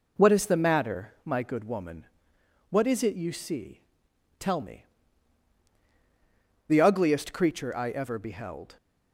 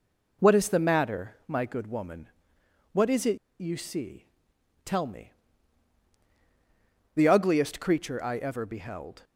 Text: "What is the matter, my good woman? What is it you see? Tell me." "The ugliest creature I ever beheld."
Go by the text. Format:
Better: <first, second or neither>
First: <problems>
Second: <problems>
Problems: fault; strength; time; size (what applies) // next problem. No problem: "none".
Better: first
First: none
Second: pauses between "it" and "you"; slight; at 3.3 s; 0.22 s long